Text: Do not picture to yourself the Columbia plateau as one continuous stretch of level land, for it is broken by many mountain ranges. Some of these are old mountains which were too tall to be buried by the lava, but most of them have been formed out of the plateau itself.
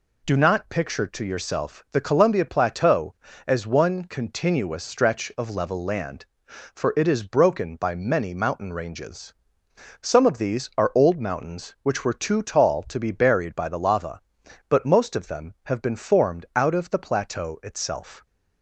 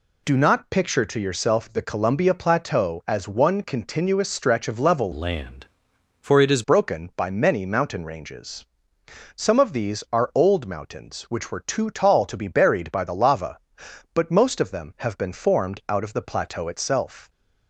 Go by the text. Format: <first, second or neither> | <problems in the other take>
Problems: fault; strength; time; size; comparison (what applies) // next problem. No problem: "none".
first | changes voice from "land" to "is"; from 5.1 to 6.6 s; 1.5 s long